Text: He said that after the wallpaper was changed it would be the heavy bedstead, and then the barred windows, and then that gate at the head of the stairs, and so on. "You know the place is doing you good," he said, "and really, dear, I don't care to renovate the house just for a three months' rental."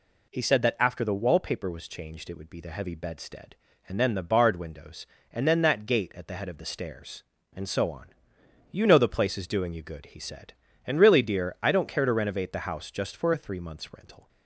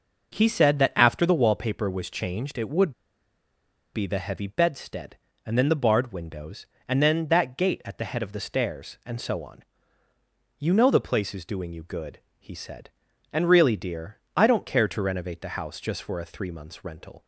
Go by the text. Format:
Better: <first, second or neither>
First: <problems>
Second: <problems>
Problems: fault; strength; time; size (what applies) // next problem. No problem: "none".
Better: first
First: none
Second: pauses between "would" and "be"; at 2.9 s; 1.0 s long